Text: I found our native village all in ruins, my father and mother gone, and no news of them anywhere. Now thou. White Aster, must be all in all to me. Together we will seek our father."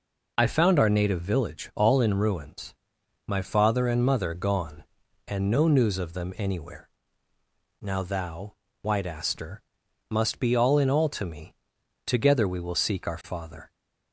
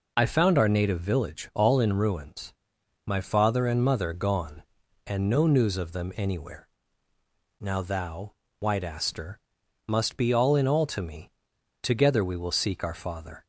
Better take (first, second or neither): neither